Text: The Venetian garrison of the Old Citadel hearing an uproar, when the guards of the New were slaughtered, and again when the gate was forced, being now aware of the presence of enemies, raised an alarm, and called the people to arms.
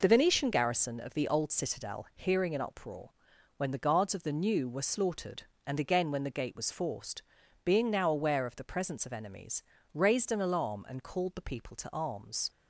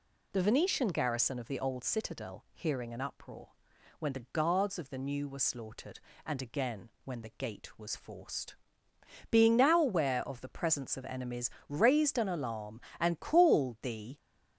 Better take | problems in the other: first | pauses between "again" and "when"; slight; at 6.8 s; 0.16 s long // stops before "people to arms"; at 14.1 s

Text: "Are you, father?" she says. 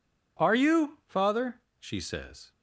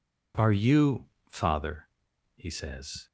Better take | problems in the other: first | says "he" for "she"; at 2.3 s

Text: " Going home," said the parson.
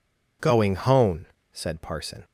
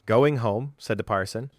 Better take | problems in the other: second | skips "the"; at 1.8 s

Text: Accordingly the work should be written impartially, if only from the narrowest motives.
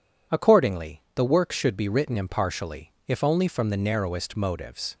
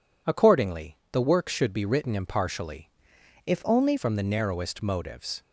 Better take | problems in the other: first | changes voice from "if" to "only"; from 3.4 to 3.9 s; 0.5 s long

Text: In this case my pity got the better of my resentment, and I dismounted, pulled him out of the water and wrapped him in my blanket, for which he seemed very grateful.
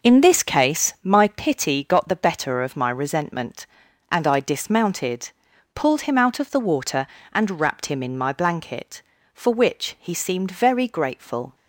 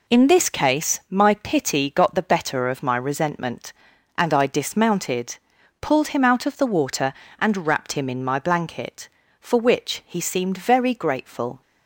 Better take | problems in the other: second | starts louder than the rest; noticeable; until 1.4 s; 5 dB

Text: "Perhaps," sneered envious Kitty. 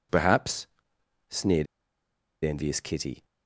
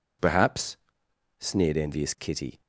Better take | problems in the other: second | pauses between "sneered" and "envious"; noticeable; at 1.6 s; 0.78 s long

